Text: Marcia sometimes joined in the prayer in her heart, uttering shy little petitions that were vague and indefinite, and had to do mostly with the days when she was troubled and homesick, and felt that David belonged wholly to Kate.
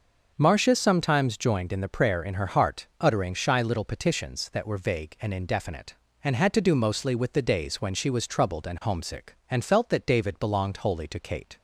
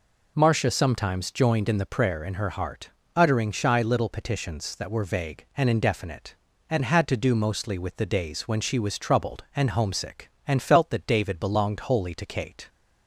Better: neither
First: none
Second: none

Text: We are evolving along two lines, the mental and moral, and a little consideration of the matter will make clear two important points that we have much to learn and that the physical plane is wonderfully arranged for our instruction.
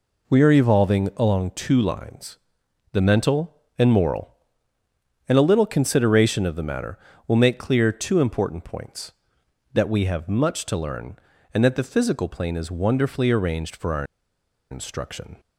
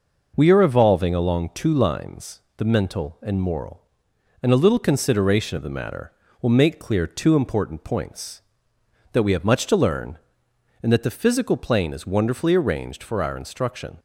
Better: second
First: pauses between "our" and "instruction"; noticeable; at 14.0 s; 0.67 s long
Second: none

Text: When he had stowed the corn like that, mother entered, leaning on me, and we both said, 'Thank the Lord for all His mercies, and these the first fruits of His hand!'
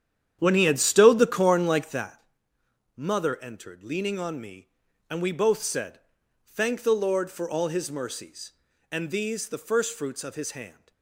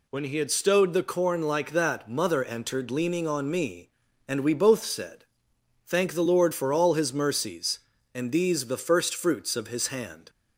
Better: second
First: starts louder than the rest; strong; until 2.1 s; 9.5 dB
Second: none

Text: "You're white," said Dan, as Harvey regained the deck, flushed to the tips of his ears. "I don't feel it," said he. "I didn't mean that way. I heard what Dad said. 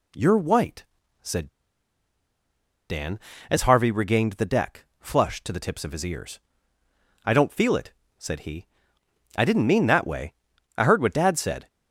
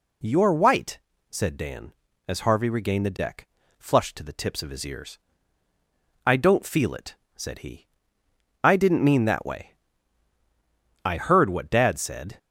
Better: second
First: pauses between "said" and "Dan"; strong; at 1.4 s; 1.4 s long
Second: none

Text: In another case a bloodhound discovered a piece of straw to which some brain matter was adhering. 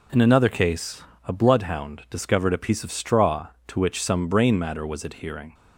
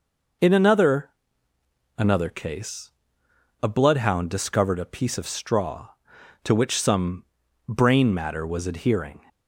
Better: first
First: pauses between "case" and "a"; slight; at 1.0 s; 0.24 s long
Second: says "another" twice; at 1.9 s // pauses between "case" and "a"; noticeable; at 2.9 s; 0.72 s long // pauses between "some" and "brain"; at 7.2 s; 0.44 s long

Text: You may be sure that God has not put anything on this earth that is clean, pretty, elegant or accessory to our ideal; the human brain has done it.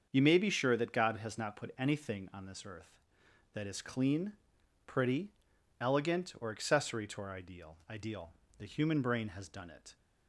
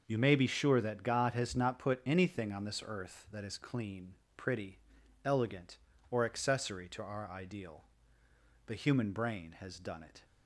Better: second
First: starts louder than the rest; until 1.1 s; 7 dB // says "ideal" twice; at 7.8 s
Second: none

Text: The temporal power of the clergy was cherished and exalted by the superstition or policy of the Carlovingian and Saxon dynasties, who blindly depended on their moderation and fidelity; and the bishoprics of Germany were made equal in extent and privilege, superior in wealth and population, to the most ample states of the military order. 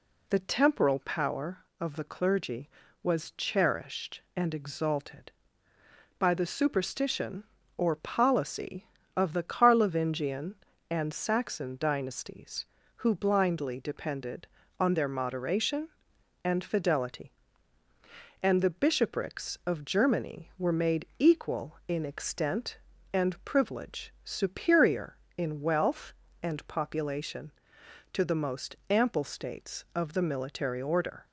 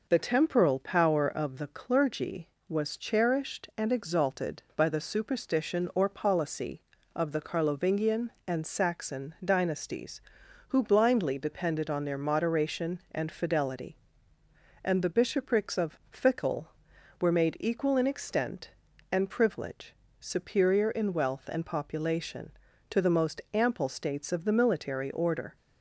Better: first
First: none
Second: says "Fickle" for "Germany"; at 16.0 s

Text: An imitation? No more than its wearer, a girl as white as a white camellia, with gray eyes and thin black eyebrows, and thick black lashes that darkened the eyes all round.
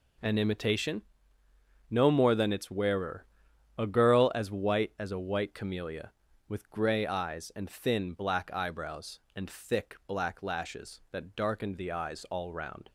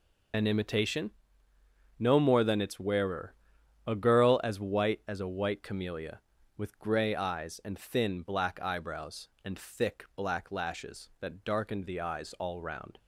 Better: first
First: none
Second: loses the start of "An"; at 0.3 s; 70 ms

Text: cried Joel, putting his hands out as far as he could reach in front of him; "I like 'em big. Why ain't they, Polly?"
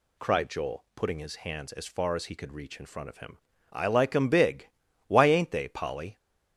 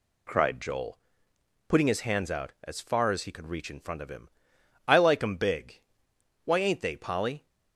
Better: second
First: skips "out"; at 1.7 s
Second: none

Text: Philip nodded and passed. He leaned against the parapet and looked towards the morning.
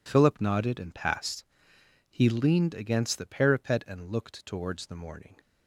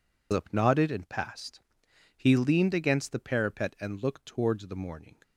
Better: first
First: none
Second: loses the start of "Philip"; at 0.3 s; 125 ms

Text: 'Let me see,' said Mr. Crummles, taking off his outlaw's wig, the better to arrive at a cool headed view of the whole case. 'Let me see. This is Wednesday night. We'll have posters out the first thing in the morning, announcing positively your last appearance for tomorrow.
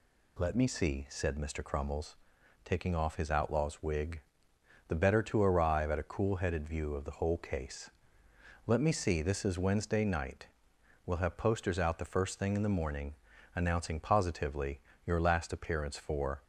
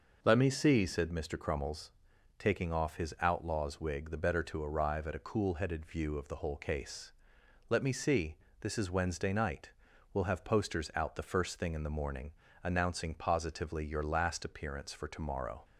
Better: second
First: pauses between "positively" and "your"; slight; at 14.7 s; 0.26 s long // stops before "tomorrow"; at 16.4 s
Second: none

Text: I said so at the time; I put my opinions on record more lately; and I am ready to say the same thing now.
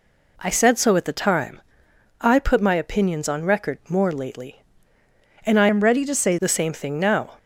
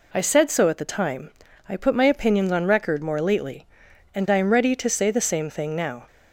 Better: second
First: changes voice from "am" to "say"; from 5.6 to 6.3 s; 0.7 s long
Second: none

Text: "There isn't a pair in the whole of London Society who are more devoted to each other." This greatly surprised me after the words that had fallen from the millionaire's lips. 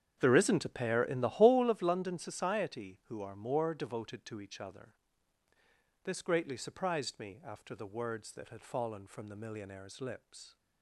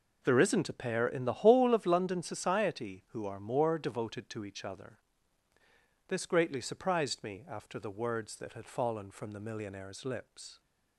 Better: second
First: starts louder than the rest; strong; until 1.7 s; 8.5 dB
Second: none

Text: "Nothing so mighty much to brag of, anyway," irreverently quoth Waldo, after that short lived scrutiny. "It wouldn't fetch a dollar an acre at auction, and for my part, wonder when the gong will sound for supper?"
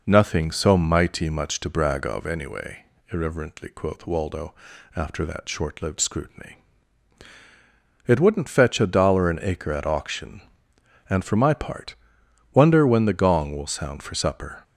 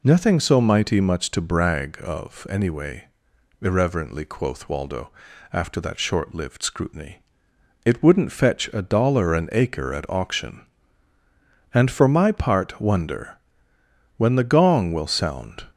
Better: first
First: none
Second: pauses between "wonder" and "when"; noticeable; at 13.3 s; 0.80 s long // stops before "for supper"; at 15.7 s

